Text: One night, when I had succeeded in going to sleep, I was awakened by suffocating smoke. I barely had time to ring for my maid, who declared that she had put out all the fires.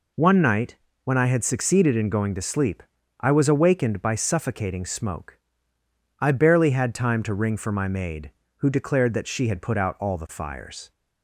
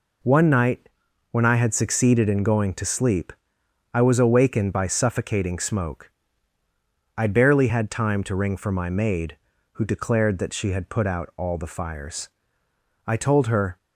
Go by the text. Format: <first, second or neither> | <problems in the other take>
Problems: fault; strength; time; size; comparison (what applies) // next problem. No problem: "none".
first | goes on to say "I told her"; noticeable; from 13.0 s on; 0.70 s long